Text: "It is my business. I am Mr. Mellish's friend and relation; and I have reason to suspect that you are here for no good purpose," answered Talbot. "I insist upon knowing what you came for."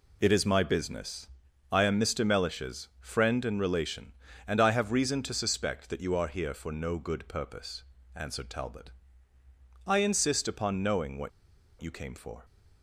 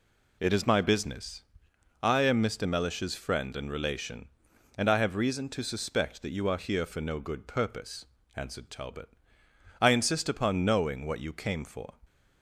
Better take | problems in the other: second | pauses between "what" and "you"; noticeable; at 11.2 s; 0.51 s long

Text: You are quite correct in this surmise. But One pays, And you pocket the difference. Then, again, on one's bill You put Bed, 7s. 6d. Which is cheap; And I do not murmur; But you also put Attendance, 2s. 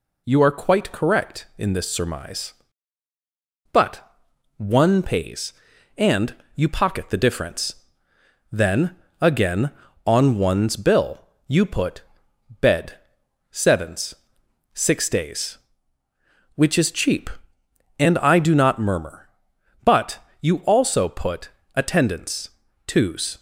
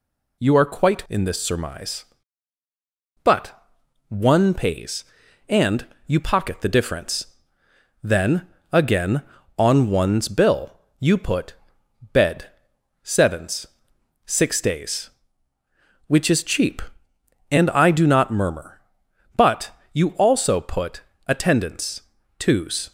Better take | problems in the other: first | skips "correct"; at 1.0 s // pauses between "But" and "One"; noticeable; at 3.5 s; 0.56 s long; noticeable in the first // pauses between "And" and "you"; slight; at 5.8 s; 0.22 s long; slight in the first // pauses between "bill" and "You"; slight; at 10.7 s; 0.22 s long; slight in the first // pauses between "put" and "Bed"; noticeable; at 11.5 s; 0.60 s long; noticeable in the first // pauses between "But" and "you"; slight; at 19.7 s; 0.20 s long; slight in the first // pauses between "put" and "Attendance"; slight; at 21.0 s; 0.26 s long; slight in the first

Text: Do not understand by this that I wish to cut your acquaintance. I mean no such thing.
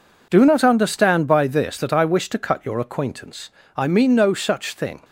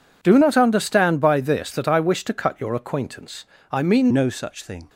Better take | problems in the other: first | changes voice at "no"; from 4.1 s on; 0.7 s long

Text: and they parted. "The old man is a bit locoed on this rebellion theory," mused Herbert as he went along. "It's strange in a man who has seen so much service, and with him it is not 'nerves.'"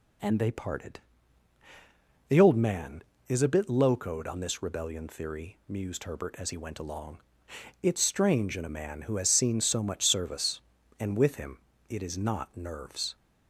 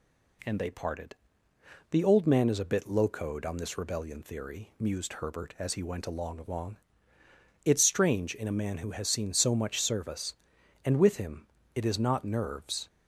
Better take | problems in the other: first | says "along" twice; at 6.3 s // pauses between "him" and "it"; slight; at 11.4 s; 0.28 s long; slight in the first

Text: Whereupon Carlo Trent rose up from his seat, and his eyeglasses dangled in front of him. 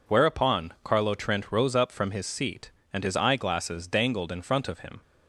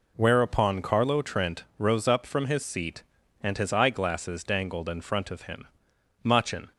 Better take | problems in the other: first | goes on to say "Machin"; from 6.2 s on; 0.52 s long

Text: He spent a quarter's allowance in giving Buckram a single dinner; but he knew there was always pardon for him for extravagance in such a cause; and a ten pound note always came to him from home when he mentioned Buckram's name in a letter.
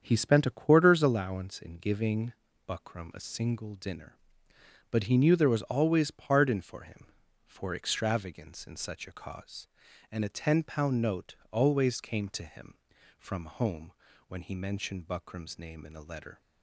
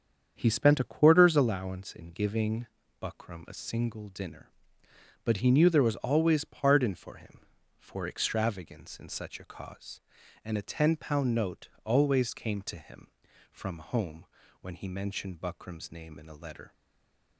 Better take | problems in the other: first | starts louder than the rest; strong; until 1.3 s; 7.5 dB; strong in the first // pauses between "giving" and "Buckram"; slight; at 2.6 s; 0.34 s long; slight in the first // pauses between "note" and "always"; slight; at 11.6 s; 0.16 s long; slight in the first // pauses between "home" and "when"; slight; at 14.2 s; 0.36 s long; slight in the first // stays silent after the last word; slight; from 16.7 s on; 0.6 s long

